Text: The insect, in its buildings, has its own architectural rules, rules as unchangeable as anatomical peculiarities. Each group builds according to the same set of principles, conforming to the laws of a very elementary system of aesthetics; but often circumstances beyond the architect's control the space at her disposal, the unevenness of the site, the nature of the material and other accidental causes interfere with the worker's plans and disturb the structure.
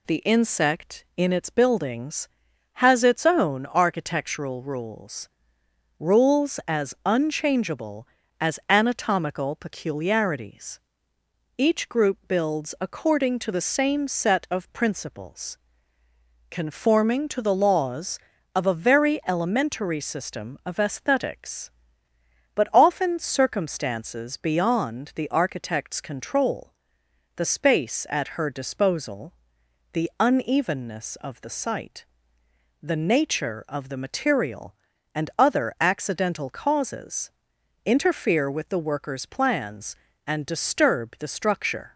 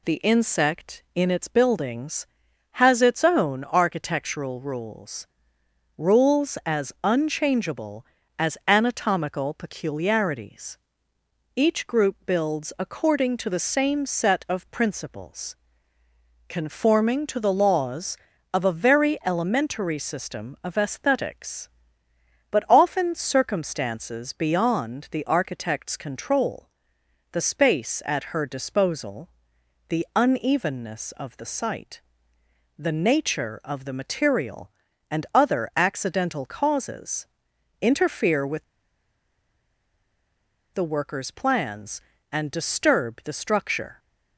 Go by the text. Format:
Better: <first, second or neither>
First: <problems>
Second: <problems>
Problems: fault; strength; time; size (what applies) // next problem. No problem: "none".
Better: first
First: pauses between "control" and "the"; noticeable; at 26.7 s; 0.64 s long // pauses between "causes" and "interfere"; noticeable; at 37.2 s; 0.56 s long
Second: pauses between "control" and "the"; noticeable; at 26.6 s; 0.64 s long // pauses between "causes" and "interfere"; noticeable; at 37.2 s; 0.56 s long // pauses between "with" and "the"; strong; at 38.6 s; 2.1 s long